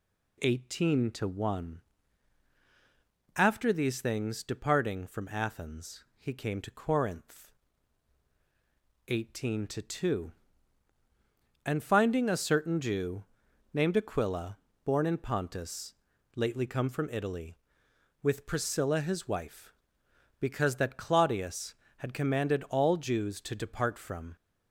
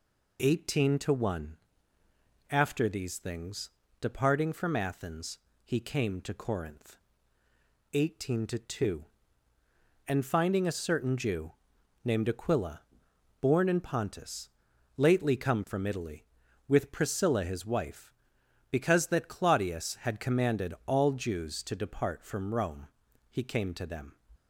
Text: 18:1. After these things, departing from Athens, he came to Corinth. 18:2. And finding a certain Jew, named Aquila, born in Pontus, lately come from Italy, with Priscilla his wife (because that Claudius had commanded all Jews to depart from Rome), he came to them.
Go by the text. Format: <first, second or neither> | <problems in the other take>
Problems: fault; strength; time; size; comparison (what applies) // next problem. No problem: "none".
second | stops before "Rome he came to them"; at 24.3 s